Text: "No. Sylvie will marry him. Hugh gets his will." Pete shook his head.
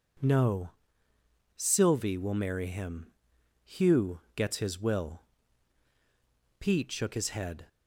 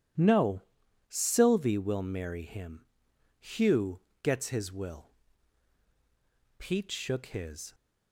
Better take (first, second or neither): first